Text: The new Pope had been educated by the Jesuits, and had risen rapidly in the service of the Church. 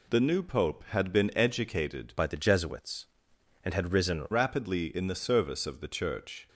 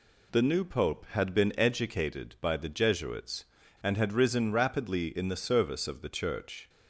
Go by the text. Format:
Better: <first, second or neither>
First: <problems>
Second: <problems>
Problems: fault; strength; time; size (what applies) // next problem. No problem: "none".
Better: second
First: changes voice from "by" to "risen"; from 2.1 to 4.2 s; 2.1 s long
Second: none